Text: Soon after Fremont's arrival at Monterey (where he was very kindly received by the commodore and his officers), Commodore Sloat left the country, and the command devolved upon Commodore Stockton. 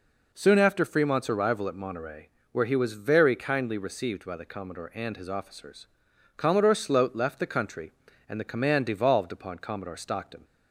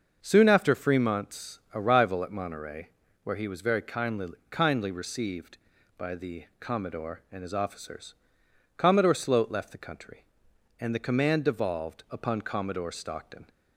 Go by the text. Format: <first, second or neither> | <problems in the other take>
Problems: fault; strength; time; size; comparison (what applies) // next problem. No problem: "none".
first | starts louder than the rest; until 1.2 s; 6 dB // says "kindly" twice; at 4.5 s